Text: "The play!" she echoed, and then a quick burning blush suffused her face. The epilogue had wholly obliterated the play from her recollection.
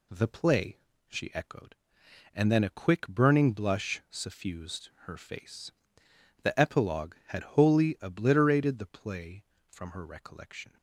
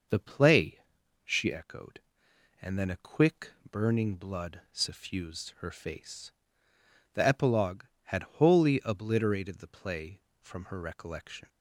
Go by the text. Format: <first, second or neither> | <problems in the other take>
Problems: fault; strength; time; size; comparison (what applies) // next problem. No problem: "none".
first | pauses between "quick" and "burning"; slight; at 3.5 s; 0.18 s long // says "blood" for "blush"; at 4.1 s // pauses between "had" and "wholly"; slight; at 8.2 s; 0.16 s long